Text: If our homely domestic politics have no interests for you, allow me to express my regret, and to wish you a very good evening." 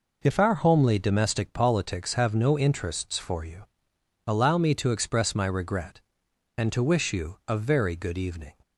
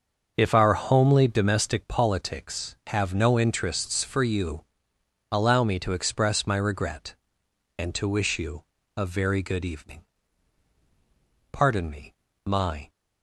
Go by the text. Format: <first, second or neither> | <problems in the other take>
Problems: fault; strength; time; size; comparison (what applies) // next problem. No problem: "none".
first | starts louder than the rest; until 1.3 s; 6.5 dB // pauses between "you" and "a"; slight; at 8.6 s; 0.32 s long // goes on to say "Pardon me my"; from 11.5 s on; 1.3 s long